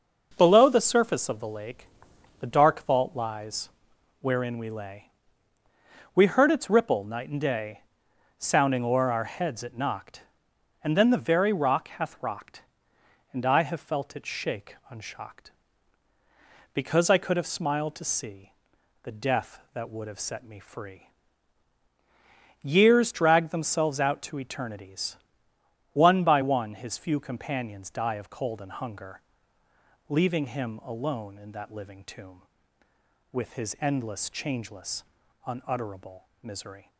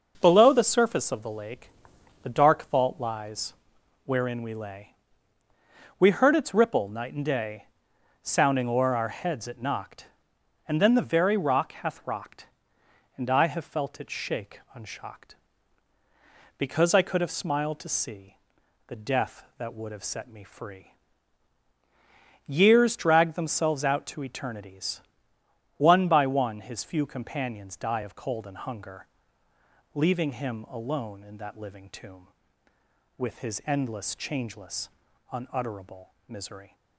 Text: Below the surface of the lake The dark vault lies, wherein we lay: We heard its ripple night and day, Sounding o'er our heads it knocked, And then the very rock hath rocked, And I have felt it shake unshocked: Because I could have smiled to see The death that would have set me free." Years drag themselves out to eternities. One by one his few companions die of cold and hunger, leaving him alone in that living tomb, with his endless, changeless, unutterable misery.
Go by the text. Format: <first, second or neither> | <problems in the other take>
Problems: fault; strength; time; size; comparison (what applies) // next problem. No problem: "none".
neither | pauses between "lake" and "The"; noticeable; the same in both // pauses between "see" and "The"; noticeable; the same in both // pauses between "unutterable" and "misery"; slight; the same in both